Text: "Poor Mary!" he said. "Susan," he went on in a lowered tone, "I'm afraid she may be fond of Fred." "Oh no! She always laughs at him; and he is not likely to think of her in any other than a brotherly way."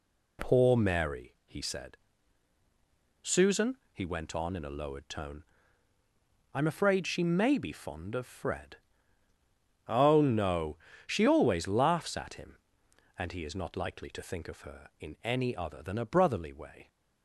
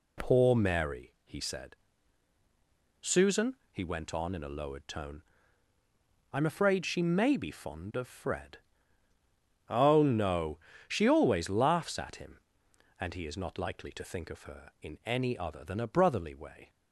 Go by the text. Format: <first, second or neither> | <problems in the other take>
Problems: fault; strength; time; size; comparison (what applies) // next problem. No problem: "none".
neither | none